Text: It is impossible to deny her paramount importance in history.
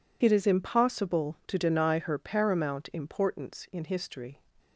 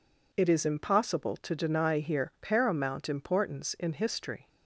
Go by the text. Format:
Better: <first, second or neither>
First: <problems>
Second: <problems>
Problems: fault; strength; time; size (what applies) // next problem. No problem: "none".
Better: first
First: none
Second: says "here" for "her"; at 1.9 s